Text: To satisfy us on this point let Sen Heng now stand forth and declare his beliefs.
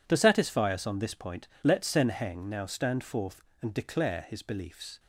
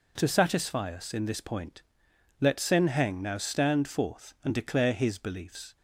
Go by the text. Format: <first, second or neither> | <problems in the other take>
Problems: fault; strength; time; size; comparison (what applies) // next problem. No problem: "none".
first | says "in" for "on"; at 1.1 s // pauses between "point" and "let"; noticeable; at 1.8 s; 0.58 s long; slight in the first